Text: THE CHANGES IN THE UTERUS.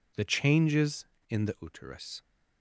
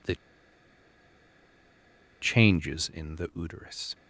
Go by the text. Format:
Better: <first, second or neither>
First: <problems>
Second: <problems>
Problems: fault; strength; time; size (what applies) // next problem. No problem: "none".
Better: first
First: none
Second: pauses between "THE" and "CHANGES"; strong; at 0.1 s; 2.0 s long